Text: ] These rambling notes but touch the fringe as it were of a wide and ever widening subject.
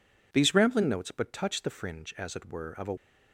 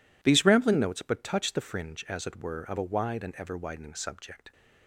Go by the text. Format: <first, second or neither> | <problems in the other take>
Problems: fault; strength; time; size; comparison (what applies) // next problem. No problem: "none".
second | stops before "wide and ever widening subject"; at 2.9 s